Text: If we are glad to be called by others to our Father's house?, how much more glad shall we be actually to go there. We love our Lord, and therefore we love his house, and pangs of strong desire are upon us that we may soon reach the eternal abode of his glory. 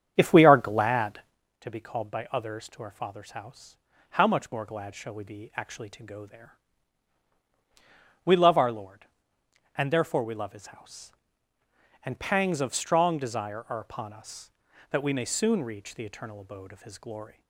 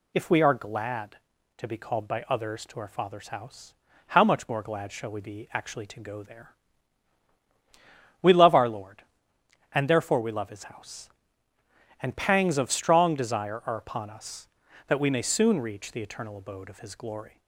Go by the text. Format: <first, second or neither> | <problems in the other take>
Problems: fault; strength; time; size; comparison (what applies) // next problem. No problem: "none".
second | starts louder than the rest; strong; until 1.4 s; 8 dB